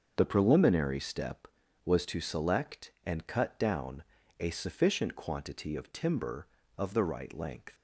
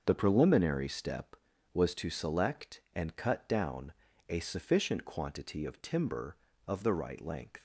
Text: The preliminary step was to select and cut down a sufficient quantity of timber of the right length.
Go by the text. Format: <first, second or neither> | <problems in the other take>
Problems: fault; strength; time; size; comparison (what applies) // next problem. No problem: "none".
neither | starts louder than the rest; the same in both // pauses between "down" and "a"; slight; the same in both